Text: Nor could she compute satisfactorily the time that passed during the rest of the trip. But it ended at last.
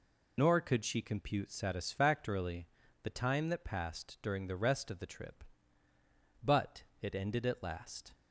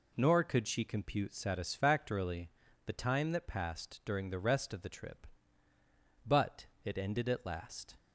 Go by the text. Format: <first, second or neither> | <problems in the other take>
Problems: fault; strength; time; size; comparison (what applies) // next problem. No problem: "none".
second | loses the start of "Nor"; at 0.3 s; 55 ms // pauses between "satisfactorily" and "the"; slight; at 2.6 s; 0.34 s long; slight in the second // pauses between "But" and "it"; slight; at 6.8 s; 0.16 s long; slight in the second